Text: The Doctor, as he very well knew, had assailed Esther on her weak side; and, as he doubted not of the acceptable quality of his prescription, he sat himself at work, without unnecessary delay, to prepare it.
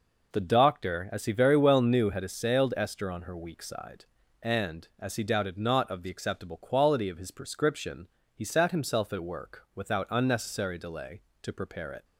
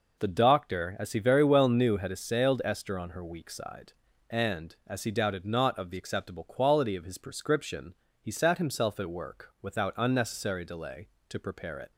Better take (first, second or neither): neither